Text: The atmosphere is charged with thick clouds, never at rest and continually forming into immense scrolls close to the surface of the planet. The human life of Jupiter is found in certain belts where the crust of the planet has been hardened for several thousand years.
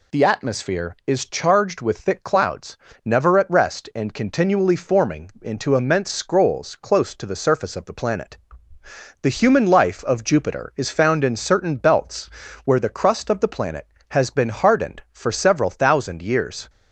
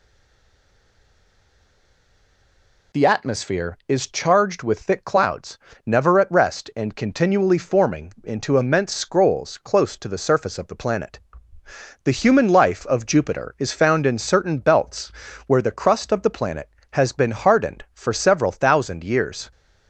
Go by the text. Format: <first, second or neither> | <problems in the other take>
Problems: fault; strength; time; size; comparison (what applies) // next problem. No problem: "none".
first | stays silent before the first word; strong; until 2.9 s; 2.9 s long // pauses between "belts" and "where"; slight; at 15.1 s; 0.36 s long; slight in the first